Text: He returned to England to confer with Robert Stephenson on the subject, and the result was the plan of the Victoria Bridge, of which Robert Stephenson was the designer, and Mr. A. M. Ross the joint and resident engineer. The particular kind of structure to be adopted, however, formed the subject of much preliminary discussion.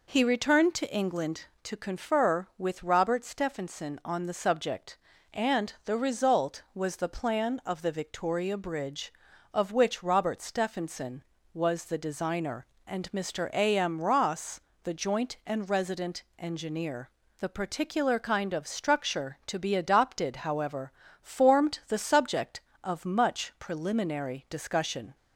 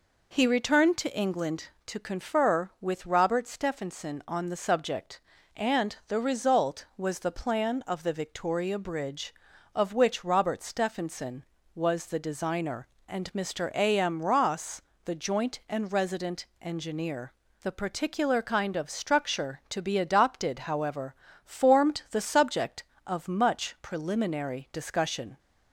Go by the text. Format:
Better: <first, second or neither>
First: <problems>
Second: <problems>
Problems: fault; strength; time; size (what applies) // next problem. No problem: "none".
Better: neither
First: pauses between "Ross" and "the"; slight; at 14.6 s; 0.22 s long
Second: pauses between "Ross" and "the"; slight; at 14.8 s; 0.22 s long